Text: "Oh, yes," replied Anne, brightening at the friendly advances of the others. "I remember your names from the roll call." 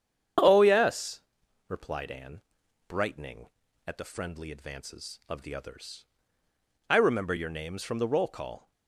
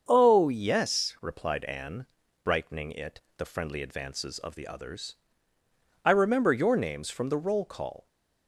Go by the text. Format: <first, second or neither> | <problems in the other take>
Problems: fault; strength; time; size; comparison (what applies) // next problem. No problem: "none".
first | starts louder than the rest; until 1.0 s; 7 dB; strong in the first // says "it" for "at"; at 2.9 s